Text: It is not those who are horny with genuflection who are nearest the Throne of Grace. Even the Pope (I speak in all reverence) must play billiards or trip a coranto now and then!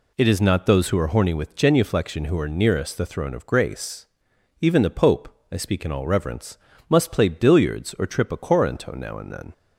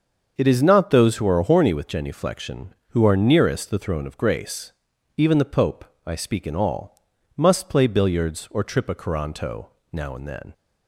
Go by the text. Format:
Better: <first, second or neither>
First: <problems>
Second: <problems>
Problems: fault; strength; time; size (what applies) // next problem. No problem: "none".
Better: first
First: none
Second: starts louder than the rest; until 1.3 s; 6.5 dB // skips "reverence"; at 7.1 s // pauses between "coranto" and "now"; slight; at 9.6 s; 0.26 s long